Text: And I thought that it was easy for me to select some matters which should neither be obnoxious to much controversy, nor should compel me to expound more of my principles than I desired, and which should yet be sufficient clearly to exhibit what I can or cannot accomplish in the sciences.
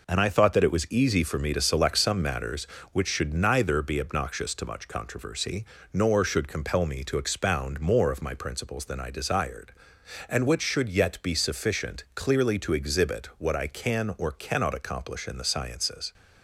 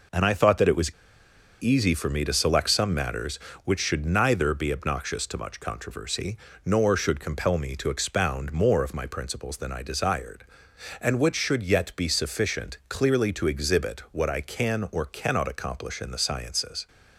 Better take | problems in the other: first | pauses between "was" and "easy"; noticeable; at 0.9 s; 0.67 s long

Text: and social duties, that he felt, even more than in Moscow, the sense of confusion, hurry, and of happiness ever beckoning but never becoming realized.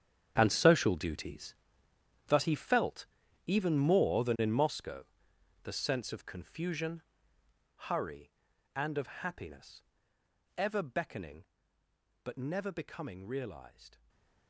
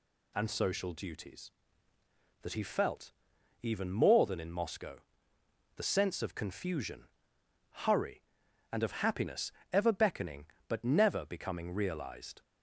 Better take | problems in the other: second | gets quieter; strong; throughout; 15.5 dB // pauses between "happiness" and "ever"; noticeable; at 9.8 s; 0.72 s long; slight in the second // stays silent after the last word; slight; from 13.9 s on; 0.5 s long

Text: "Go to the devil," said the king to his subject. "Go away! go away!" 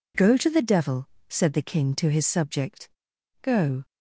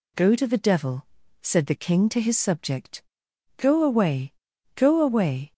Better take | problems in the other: second | stops before "away go away"; at 3.8 s

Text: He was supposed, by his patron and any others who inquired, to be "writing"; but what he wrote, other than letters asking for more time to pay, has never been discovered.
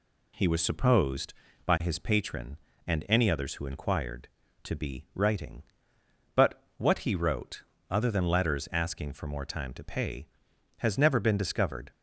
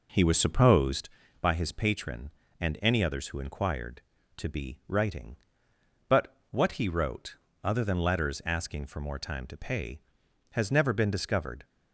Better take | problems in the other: first | starts louder than the rest; noticeable; until 1.1 s; 4.5 dB

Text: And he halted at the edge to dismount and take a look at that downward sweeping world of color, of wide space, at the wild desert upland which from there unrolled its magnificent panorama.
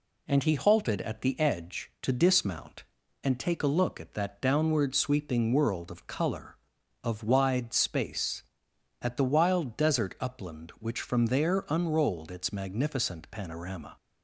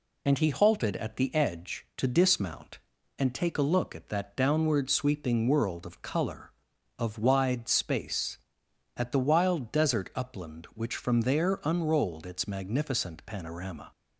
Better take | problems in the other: first | loses the start of "And"; at 0.2 s; 25 ms

